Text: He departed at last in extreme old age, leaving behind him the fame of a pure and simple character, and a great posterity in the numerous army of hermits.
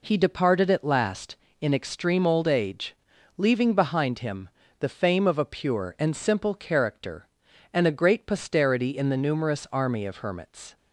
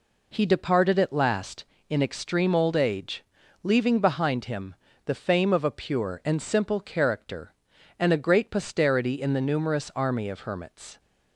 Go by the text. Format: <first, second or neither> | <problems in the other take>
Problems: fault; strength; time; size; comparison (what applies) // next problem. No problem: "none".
neither | pauses between "him" and "the"; slight; the same in both